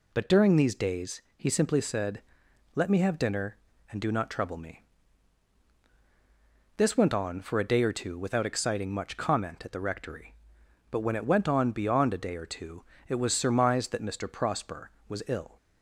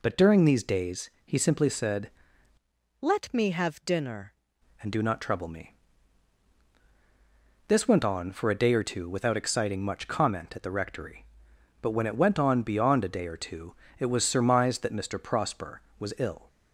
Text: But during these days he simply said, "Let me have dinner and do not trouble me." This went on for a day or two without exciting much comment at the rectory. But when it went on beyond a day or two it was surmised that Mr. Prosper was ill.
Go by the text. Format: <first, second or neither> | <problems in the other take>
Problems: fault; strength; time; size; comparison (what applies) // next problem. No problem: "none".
first | changes voice from "Let" to "dinner"; from 2.9 to 4.3 s; 1.4 s long // pauses between "two" and "it"; slight; at 13.7 s; 0.26 s long; slight in the first